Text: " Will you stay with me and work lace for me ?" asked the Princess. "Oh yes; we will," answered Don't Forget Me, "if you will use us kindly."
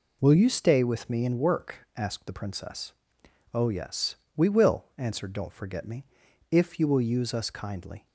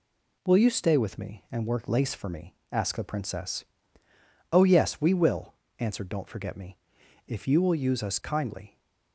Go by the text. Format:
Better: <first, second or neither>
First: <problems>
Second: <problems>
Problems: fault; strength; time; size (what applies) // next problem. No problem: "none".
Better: second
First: skips "lace for me"; at 1.8 s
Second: none